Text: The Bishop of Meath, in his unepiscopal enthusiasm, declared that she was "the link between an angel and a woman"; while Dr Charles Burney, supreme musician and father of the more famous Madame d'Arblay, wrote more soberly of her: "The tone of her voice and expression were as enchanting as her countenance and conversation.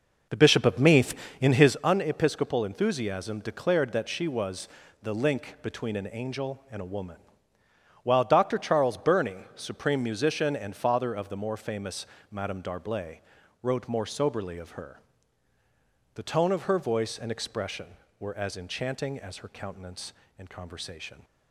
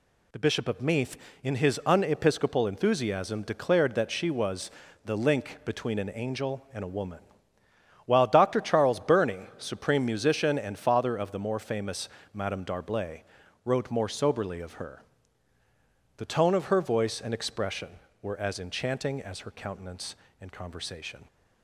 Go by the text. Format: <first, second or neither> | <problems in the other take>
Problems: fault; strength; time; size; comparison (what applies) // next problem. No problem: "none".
second | starts louder than the rest; noticeable; until 1.8 s; 5.5 dB // pauses between "was" and "the"; slight; at 4.6 s; 0.34 s long; slight in the second // pauses between "famous" and "Madame"; slight; at 12.0 s; 0.26 s long; slight in the second